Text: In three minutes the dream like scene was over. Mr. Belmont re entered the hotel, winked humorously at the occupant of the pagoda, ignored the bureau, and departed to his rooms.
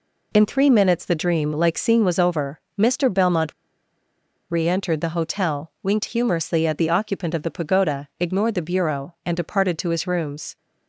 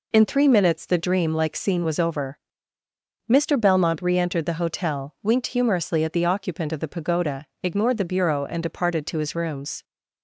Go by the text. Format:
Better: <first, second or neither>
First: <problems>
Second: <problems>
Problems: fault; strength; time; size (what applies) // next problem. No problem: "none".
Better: second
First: pauses between "Belmont" and "re"; noticeable; at 3.5 s; 0.97 s long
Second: none